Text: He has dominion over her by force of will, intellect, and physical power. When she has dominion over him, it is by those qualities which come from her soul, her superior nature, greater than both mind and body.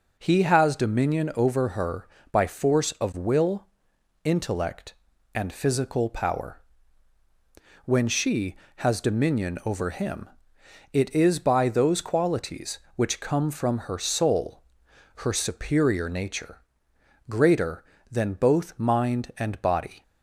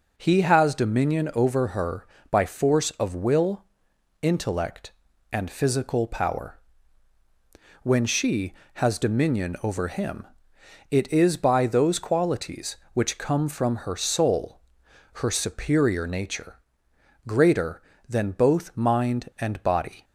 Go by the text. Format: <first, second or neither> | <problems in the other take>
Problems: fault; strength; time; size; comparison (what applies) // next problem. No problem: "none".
neither | none